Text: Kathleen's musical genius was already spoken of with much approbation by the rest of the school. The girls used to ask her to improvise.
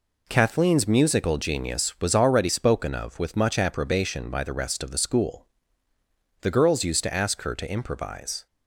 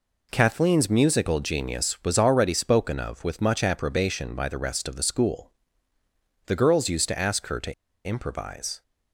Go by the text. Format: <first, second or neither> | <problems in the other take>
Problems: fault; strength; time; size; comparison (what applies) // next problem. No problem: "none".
first | pauses between "to" and "improvise"; slight; at 7.7 s; 0.32 s long